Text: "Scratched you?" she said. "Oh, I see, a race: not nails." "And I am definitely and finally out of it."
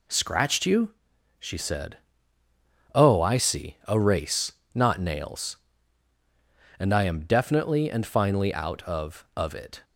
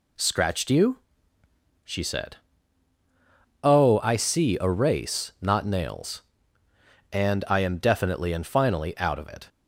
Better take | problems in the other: second | says "of" twice; at 9.3 s

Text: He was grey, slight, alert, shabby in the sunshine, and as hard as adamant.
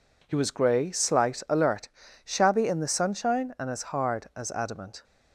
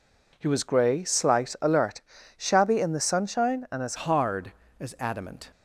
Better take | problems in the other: first | changes voice at "hard"; from 3.9 s on; 1.6 s long

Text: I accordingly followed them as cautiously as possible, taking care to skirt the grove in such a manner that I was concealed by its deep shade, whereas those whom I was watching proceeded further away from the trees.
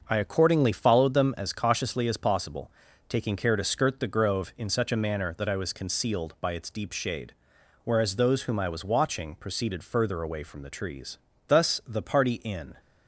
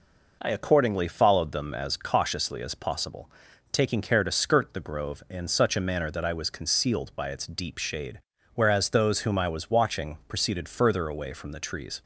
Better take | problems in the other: second | starts louder than the rest; noticeable; until 1.0 s; 6 dB // goes on to say "Thus the party in"; noticeable; from 11.4 s on; 1.2 s long

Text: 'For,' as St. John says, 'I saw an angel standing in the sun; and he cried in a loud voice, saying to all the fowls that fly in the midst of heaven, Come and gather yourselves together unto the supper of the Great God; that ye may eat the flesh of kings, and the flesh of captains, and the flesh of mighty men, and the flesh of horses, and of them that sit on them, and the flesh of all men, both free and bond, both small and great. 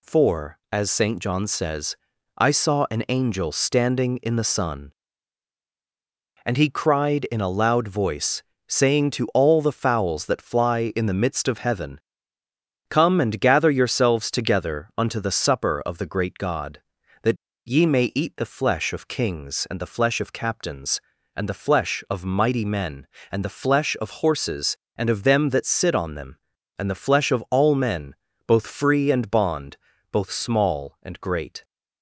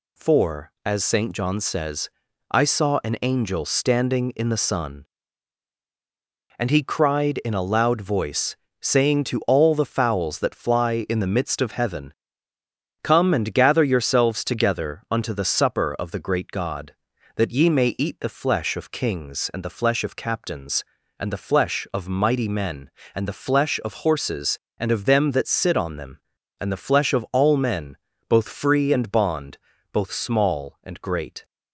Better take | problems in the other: second | pauses between "that" and "ye"; slight; at 17.3 s; 0.31 s long

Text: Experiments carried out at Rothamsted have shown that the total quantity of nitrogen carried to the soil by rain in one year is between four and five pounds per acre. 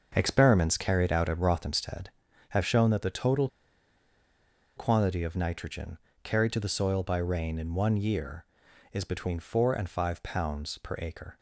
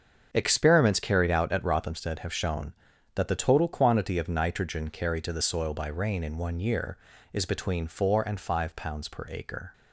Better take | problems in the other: second | starts louder than the rest; until 1.1 s; 6.5 dB; also in the second // pauses between "total" and "quantity"; strong; at 3.4 s; 1.2 s long // pauses between "nitrogen" and "carried"; slight; at 5.9 s; 0.26 s long

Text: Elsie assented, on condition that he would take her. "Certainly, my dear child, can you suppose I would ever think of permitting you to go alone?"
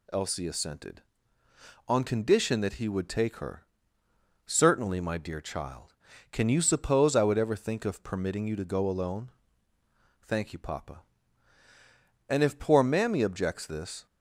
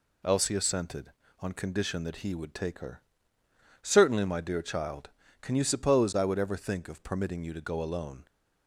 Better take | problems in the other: second | goes on to say "Thank you papa And if poor mammy objects this"; strong; from 10.2 s on; 3.8 s long

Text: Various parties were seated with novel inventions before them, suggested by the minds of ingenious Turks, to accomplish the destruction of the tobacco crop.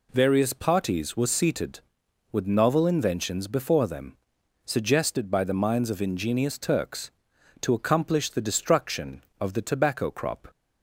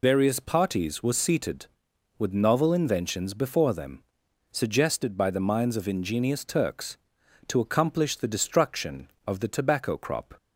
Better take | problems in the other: first | loses the start of "Various"; at 0.0 s; 70 ms

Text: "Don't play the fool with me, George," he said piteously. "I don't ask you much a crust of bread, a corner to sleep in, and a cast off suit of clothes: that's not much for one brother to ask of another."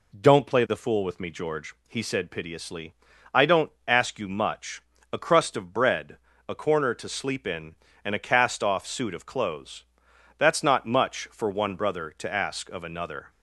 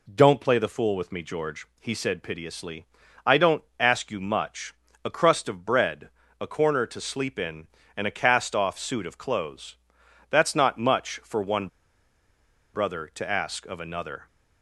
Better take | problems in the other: first | pauses between "don't" and "ask"; slight; at 3.6 s; 0.16 s long; slight in the first // pauses between "much" and "a"; slight; at 4.7 s; 0.28 s long; slight in the first // pauses between "one" and "brother"; at 11.6 s; 1.0 s long

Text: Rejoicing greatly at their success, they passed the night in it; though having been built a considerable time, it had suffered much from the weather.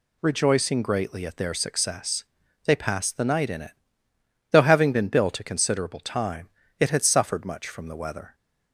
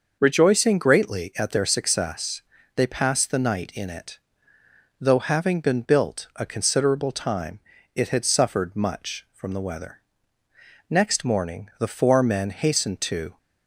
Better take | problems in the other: first | starts louder than the rest; noticeable; until 1.2 s; 6 dB // goes on to say "Next morning the four men hastened to"; strong; from 10.8 s on; 2.4 s long

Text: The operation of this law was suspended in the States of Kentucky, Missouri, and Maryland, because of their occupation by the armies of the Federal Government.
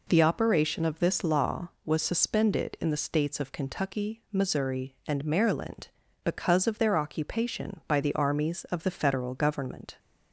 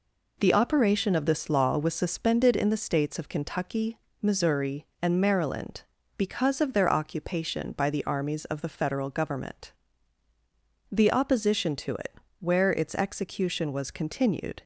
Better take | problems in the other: first | goes on to say "The opposition to it where its execution was continued"; strong; from 10.9 s on; 3.7 s long

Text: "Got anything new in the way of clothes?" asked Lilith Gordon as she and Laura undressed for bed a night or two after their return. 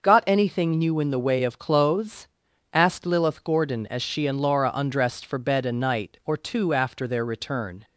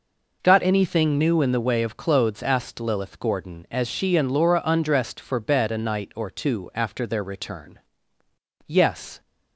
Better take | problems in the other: first | goes on to say "Yes"; from 8.6 s on; 0.54 s long

